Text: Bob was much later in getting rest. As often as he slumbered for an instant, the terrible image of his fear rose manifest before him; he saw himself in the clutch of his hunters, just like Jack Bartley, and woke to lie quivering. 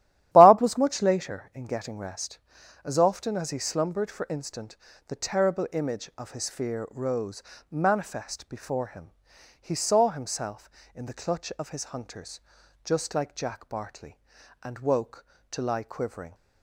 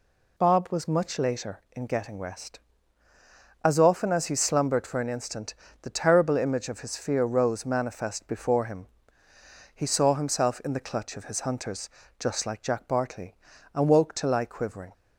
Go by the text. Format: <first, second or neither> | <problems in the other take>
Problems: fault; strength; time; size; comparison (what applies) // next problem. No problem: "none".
second | starts louder than the rest; strong; until 1.3 s; 12 dB // skips "an"; at 4.2 s // pauses between "rose" and "manifest"; slight; at 7.4 s; 0.28 s long